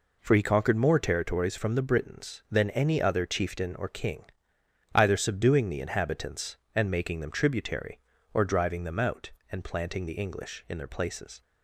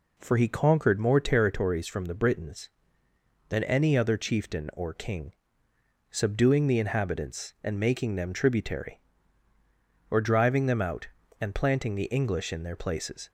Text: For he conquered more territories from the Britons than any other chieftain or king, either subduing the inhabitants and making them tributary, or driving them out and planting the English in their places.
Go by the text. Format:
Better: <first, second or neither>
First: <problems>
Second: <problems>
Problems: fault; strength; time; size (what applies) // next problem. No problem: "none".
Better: first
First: none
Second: skips "either"; at 5.7 s